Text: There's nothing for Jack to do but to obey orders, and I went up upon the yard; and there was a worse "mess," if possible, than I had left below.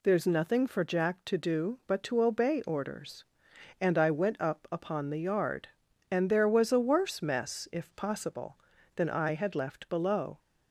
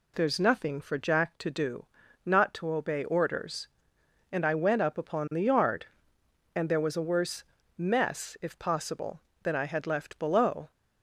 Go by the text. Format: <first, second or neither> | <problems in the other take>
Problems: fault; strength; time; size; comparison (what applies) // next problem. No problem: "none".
first | says "not" for "but"; at 2.2 s // pauses between "worse" and "mess"; slight; at 7.4 s; 0.34 s long